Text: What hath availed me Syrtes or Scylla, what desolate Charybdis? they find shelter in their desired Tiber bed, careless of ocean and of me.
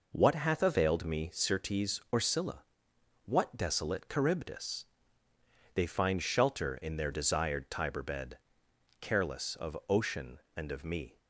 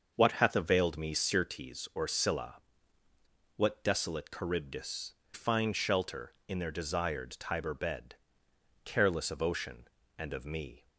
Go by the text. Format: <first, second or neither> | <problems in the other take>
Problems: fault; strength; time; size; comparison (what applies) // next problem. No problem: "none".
first | starts louder than the rest; until 1.1 s; 6.5 dB // skips "they"; at 5.2 s